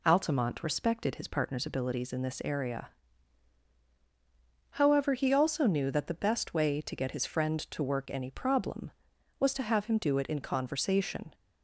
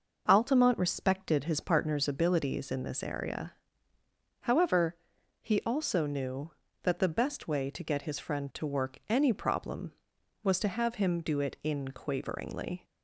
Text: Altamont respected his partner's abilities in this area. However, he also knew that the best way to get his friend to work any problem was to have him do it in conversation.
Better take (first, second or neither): first